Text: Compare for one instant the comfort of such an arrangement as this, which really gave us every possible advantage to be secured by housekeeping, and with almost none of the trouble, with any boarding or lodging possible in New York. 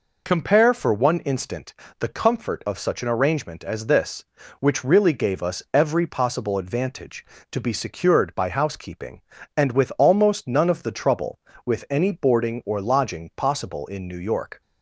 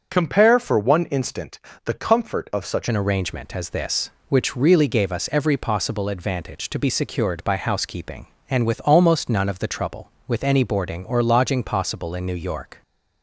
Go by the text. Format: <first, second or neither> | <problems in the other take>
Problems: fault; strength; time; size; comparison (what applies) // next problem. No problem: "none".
first | pauses between "instant" and "the"; slight; at 1.5 s; 0.28 s long; slight in the first // changes voice at "an"; from 2.8 s on; 10.0 s long